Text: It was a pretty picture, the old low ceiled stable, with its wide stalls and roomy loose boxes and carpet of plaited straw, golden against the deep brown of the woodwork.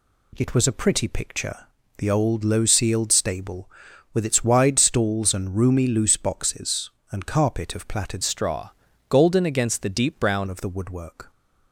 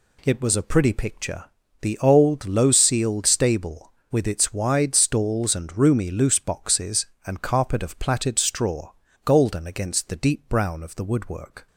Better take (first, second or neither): second